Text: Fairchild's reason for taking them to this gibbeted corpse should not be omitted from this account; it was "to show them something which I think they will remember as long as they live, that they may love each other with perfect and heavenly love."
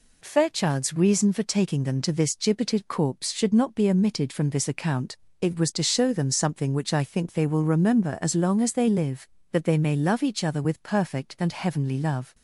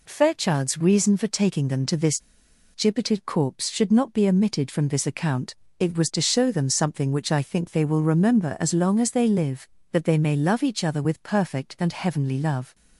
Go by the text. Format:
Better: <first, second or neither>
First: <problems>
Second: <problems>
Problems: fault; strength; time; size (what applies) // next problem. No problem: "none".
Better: first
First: none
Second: pauses between "this" and "gibbeted"; noticeable; at 2.1 s; 0.54 s long